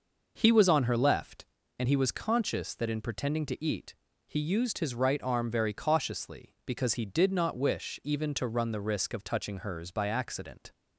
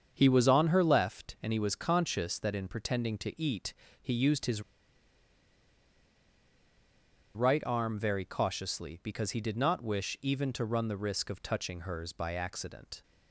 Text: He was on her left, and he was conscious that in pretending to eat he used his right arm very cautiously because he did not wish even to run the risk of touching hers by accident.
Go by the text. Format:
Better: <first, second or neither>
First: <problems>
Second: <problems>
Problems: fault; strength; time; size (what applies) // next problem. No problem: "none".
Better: first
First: pauses between "eat" and "he"; slight; at 3.9 s; 0.34 s long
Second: starts louder than the rest; strong; until 1.1 s; 7 dB // pauses between "eat" and "he"; slight; at 3.7 s; 0.28 s long // pauses between "his" and "right"; strong; at 4.6 s; 2.7 s long